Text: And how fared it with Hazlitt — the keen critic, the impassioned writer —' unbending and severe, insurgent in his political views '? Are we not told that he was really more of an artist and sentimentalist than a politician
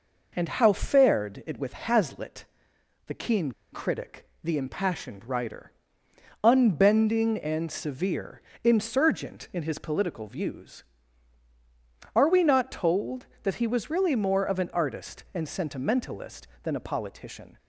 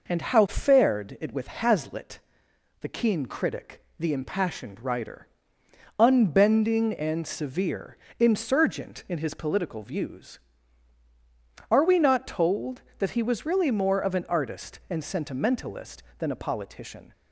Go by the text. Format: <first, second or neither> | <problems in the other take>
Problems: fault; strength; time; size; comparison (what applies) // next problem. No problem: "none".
second | pauses between "keen" and "critic"; slight; at 3.5 s; 0.20 s long